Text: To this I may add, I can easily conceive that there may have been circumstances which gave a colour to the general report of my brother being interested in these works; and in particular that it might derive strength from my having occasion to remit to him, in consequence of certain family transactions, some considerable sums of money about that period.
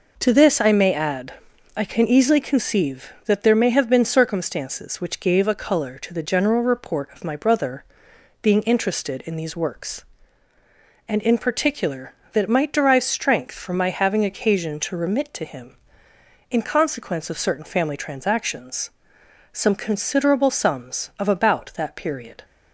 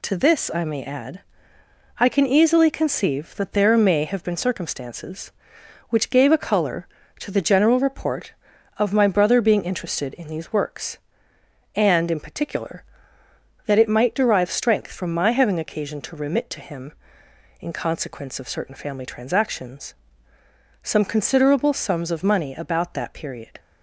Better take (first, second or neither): second